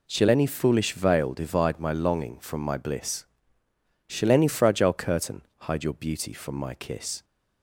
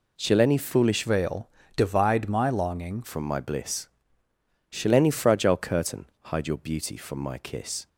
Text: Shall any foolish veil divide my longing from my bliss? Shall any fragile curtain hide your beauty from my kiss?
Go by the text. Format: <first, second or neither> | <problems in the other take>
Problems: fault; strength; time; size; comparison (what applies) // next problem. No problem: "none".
first | changes voice from "veil" to "longing"; from 1.0 to 3.0 s; 2.0 s long // pauses between "veil" and "divide"; slight; at 1.4 s; 0.26 s long // pauses between "curtain" and "hide"; slight; at 6.0 s; 0.20 s long; slight in the first